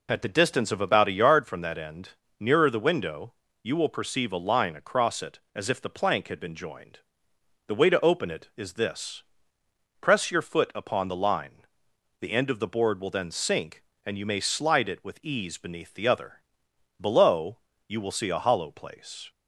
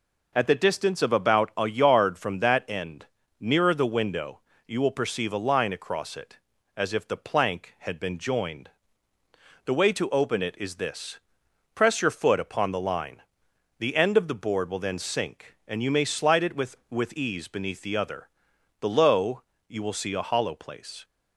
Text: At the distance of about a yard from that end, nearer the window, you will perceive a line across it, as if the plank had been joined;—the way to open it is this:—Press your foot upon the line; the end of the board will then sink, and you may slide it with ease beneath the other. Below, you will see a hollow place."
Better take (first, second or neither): first